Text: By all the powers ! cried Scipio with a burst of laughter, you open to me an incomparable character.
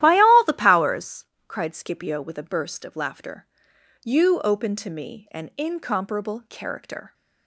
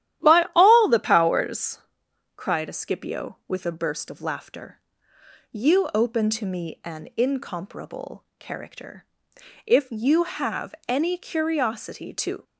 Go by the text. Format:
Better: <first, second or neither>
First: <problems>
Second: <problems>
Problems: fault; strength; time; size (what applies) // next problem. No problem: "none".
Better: first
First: starts louder than the rest; strong; until 1.0 s; 13 dB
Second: starts louder than the rest; strong; until 1.3 s; 12.5 dB // goes on to say "If you have any curiosity to"; strong; from 9.6 s on; 2.7 s long